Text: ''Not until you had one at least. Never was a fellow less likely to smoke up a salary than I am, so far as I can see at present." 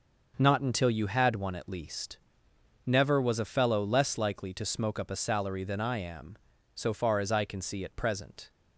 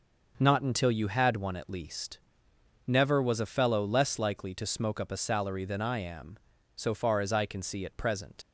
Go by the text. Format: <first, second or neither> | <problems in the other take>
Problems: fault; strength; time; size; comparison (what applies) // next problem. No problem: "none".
first | starts louder than the rest; noticeable; until 1.3 s; 6 dB; also in the first // leaves "present" unfinished; at 8.4 s; 100 ms